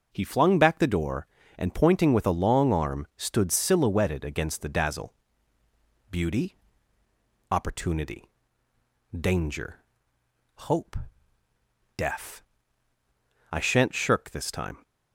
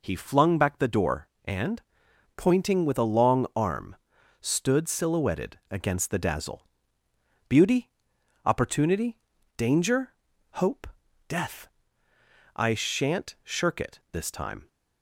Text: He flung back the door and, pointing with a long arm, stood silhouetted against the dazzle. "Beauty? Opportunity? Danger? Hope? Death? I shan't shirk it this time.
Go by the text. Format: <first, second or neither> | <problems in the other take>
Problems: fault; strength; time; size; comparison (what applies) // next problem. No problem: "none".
second | skips "it"; at 14.2 s